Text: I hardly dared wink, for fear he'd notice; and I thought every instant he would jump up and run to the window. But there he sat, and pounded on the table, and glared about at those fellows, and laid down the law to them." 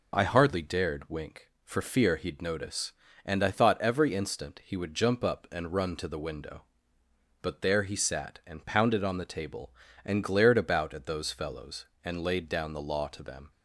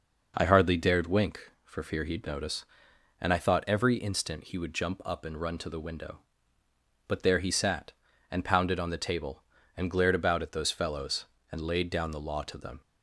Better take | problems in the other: neither | none

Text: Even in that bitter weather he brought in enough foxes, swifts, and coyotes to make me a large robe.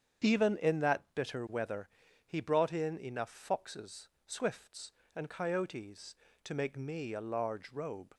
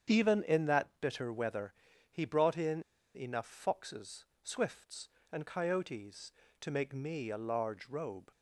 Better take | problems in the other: first | starts louder than the rest; strong; until 1.2 s; 8 dB; strong in the first // pauses between "weather" and "he"; slight; at 1.7 s; 0.36 s long; slight in the first // pauses between "in" and "enough"; slight; at 2.8 s; 0.32 s long

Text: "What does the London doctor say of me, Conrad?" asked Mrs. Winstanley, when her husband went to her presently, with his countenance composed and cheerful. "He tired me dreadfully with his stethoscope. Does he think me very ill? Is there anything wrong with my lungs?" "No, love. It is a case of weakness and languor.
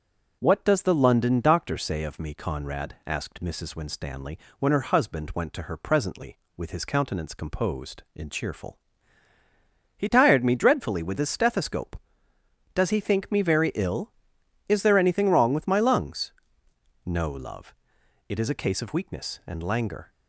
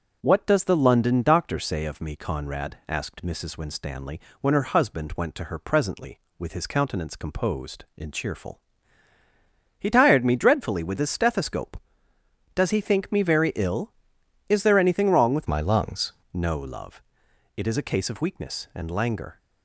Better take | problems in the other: first | changes voice from "my" to "lungs"; from 15.4 to 16.1 s; 0.7 s long

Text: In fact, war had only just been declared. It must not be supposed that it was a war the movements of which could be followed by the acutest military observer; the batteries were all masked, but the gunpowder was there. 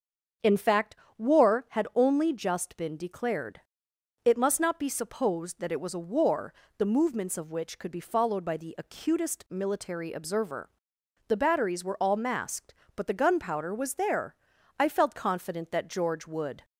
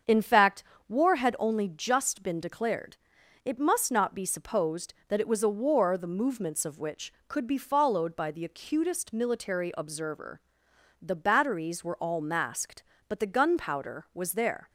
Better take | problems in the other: second | starts louder than the rest; until 1.6 s; 7 dB; strong in the second // pauses between "war" and "the"; slight; at 6.5 s; 0.24 s long // goes on to say "I felt confident that George would"; strong; from 14.8 s on; 1.8 s long

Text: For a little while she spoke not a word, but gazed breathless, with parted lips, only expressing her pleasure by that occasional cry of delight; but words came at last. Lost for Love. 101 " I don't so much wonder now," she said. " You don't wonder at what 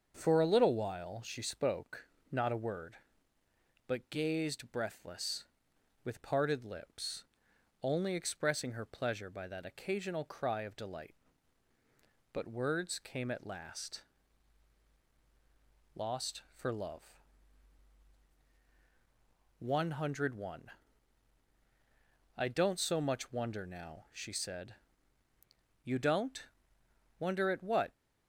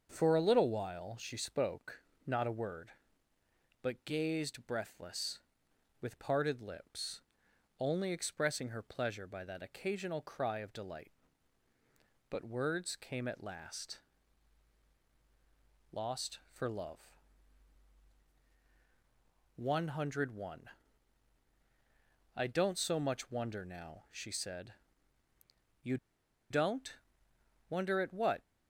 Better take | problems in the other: first | starts louder than the rest; until 1.1 s; 6.5 dB; also in the first // pauses between "spoke" and "not"; slight; at 2.0 s; 0.24 s long; slight in the first // pauses between "You" and "don't"; noticeable; at 25.9 s; 0.54 s long // pauses between "don't" and "wonder"; noticeable; at 26.9 s; 0.74 s long; noticeable in the first

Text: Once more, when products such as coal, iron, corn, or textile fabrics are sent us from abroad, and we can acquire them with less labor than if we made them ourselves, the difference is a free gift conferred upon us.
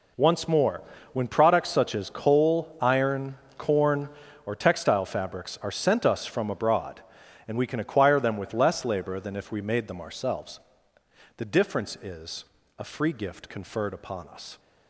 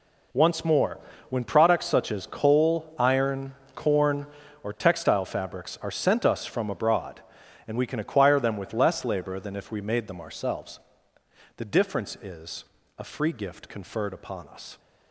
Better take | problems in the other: neither | pauses between "is" and "a"; slight; the same in both

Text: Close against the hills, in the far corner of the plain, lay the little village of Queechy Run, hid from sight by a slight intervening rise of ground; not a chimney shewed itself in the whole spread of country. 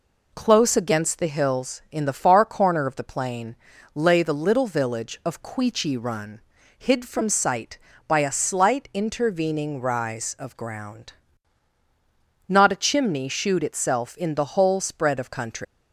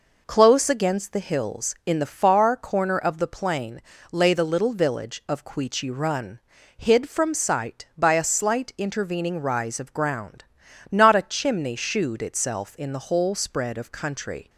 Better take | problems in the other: second | leaves "country" unfinished; at 15.6 s; 175 ms

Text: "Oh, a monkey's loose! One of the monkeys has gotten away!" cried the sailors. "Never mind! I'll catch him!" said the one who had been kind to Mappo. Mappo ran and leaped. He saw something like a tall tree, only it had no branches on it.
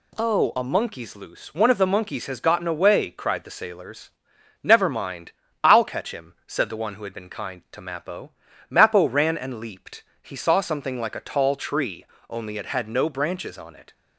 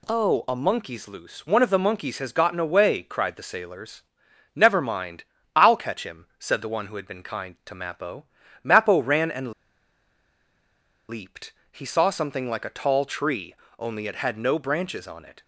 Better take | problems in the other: first | pauses between "and" and "leaped"; strong; at 9.5 s; 1.5 s long

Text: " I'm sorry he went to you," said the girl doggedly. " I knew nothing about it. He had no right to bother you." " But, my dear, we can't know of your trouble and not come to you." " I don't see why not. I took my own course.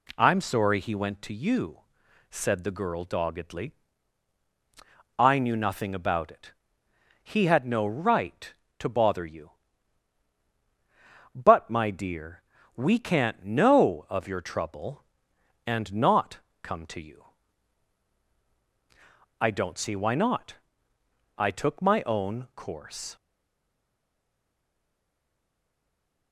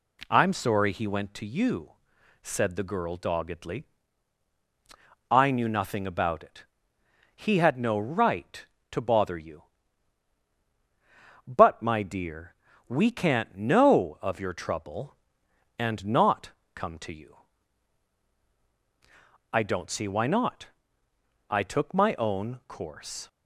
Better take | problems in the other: second | pauses between "not" and "come"; slight; at 16.3 s; 0.22 s long; slight in the second // stays silent after the last word; strong; from 23.1 s on; 3.2 s long

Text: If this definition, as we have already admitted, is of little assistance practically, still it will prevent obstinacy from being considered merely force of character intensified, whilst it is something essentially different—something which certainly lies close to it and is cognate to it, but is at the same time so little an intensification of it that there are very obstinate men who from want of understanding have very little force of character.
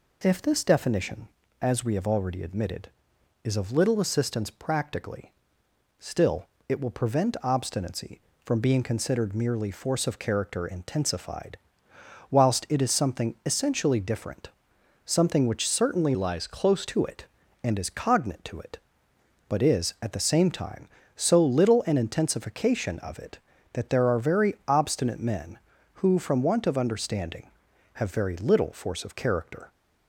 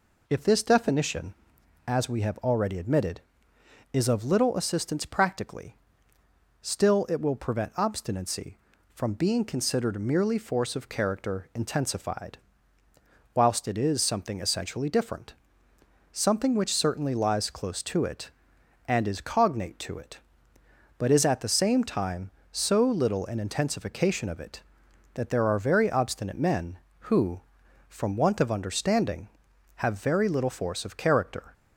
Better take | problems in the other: second | pauses between "still" and "it"; slight; at 6.4 s; 0.22 s long // changes voice from "lies" to "close"; from 16.1 to 16.8 s; 0.7 s long

